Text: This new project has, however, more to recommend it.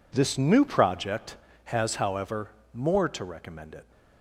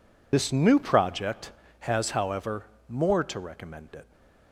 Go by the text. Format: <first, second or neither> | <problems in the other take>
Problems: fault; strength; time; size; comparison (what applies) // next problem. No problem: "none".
first | loses the start of "This"; at 0.3 s; 55 ms